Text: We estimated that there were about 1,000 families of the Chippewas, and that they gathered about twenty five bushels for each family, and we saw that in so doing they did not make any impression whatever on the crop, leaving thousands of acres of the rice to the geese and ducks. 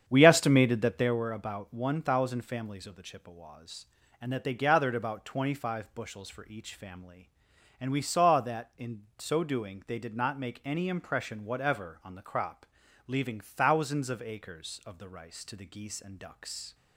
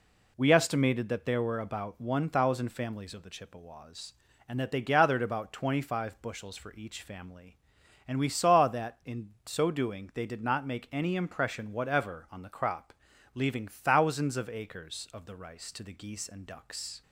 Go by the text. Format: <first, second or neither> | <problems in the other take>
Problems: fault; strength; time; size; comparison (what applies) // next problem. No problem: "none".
second | starts louder than the rest; strong; until 1.3 s; 8.5 dB